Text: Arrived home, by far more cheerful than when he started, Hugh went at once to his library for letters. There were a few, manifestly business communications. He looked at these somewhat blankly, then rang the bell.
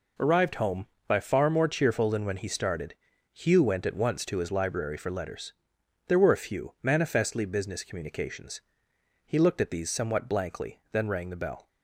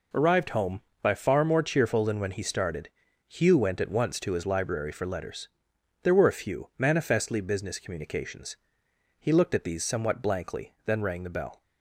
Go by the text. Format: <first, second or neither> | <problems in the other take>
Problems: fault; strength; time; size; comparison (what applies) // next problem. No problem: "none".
neither | none